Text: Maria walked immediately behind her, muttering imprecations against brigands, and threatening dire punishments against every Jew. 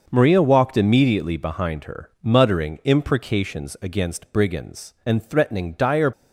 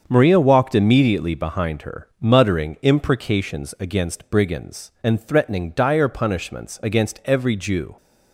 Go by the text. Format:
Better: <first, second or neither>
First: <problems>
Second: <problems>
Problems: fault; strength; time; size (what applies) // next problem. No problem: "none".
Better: second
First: starts louder than the rest; until 1.0 s; 6 dB // stops before "punishments against every Jew"; at 6.1 s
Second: starts louder than the rest; until 1.0 s; 7 dB